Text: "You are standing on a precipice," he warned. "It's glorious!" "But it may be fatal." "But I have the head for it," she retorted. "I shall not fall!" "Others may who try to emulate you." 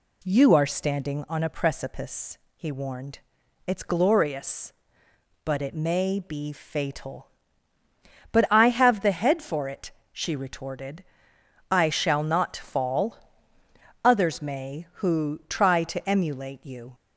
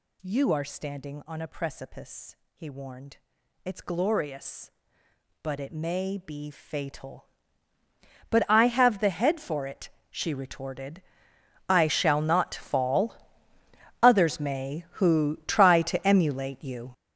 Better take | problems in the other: first | gets louder; strong; throughout; 12.5 dB

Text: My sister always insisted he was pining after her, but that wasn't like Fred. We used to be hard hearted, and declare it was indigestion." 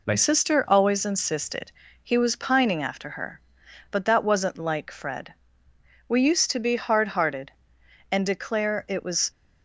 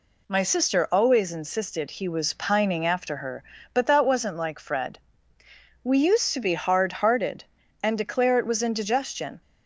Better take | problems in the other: second | pauses between "insisted" and "he"; slight; at 1.7 s; 0.30 s long // stops before "indigestion"; at 9.3 s

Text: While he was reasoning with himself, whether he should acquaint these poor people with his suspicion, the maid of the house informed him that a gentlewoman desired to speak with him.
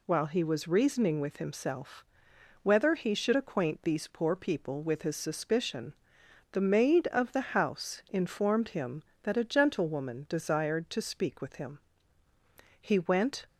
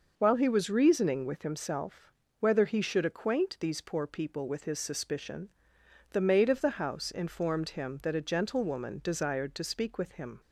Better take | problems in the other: second | goes on to say "He went"; noticeable; from 12.7 s on; 0.68 s long

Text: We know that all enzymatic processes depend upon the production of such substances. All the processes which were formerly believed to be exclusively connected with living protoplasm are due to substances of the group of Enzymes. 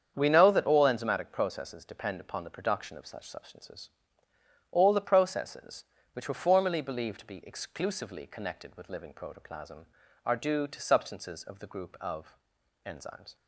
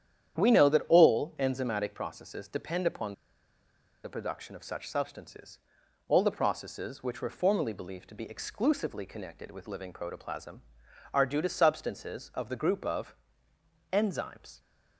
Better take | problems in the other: first | starts louder than the rest; strong; until 1.4 s; 9.5 dB; strong in the first // pauses between "upon" and "the"; noticeable; at 3.1 s; 0.89 s long // pauses between "of" and "Enzymes"; noticeable; at 13.1 s; 0.76 s long; noticeable in the first

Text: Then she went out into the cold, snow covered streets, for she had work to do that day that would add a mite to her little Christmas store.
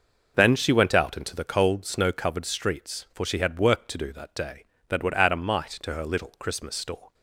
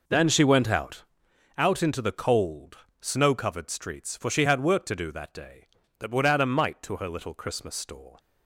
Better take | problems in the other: first | says "out" twice; at 1.5 s

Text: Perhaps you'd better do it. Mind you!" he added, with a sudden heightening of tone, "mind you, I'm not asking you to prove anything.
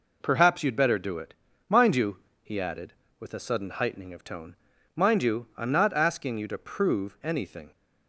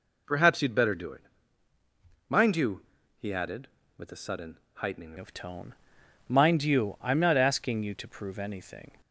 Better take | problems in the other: first | pauses between "sudden" and "heightening"; slight; at 4.5 s; 0.18 s long // changes voice at "of"; from 5.1 s on; 3.8 s long

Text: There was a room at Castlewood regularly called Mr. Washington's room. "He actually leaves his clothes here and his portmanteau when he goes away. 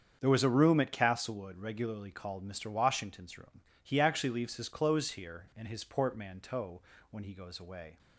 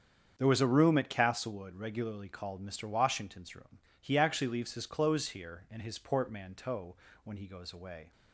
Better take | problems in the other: neither | starts louder than the rest; strong; the same in both // pauses between "portmanteau" and "when"; slight; the same in both

